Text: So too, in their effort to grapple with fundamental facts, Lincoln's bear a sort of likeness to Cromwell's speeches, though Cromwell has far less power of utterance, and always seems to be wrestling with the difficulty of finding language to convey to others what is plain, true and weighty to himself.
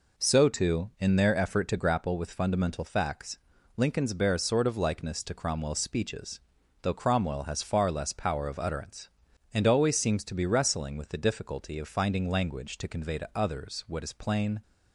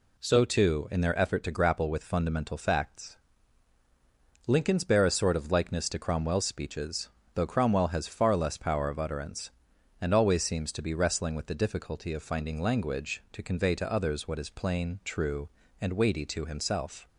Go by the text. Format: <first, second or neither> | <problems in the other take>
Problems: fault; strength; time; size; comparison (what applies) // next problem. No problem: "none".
second | stops before "true and weighty to himself"; at 14.6 s